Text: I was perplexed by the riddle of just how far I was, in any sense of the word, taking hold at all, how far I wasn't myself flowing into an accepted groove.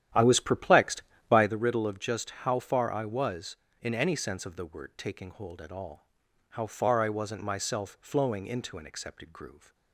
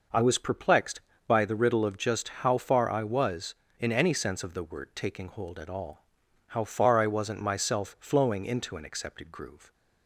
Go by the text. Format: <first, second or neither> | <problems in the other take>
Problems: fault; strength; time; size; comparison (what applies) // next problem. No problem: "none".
second | starts louder than the rest; strong; until 1.6 s; 11 dB